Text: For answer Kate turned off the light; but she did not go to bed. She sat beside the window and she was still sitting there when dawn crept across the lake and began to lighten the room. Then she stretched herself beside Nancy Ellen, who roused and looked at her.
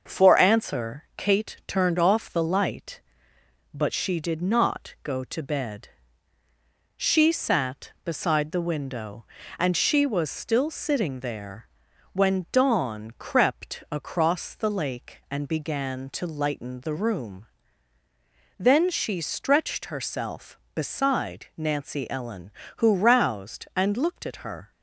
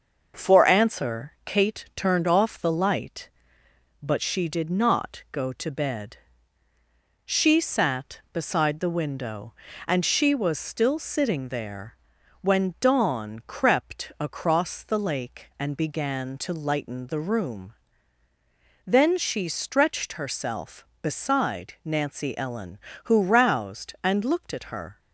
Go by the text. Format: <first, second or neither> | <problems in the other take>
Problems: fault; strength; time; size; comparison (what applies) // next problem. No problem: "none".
neither | starts louder than the rest; the same in both // pauses between "there" and "when"; noticeable; the same in both